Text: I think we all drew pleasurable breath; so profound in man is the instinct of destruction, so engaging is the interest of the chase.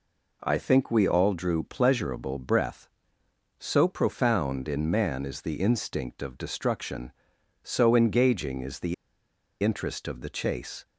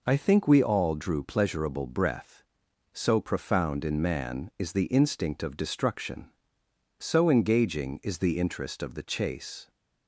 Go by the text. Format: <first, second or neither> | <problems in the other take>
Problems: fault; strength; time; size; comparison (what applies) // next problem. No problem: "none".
second | pauses between "the" and "interest"; noticeable; at 8.9 s; 0.68 s long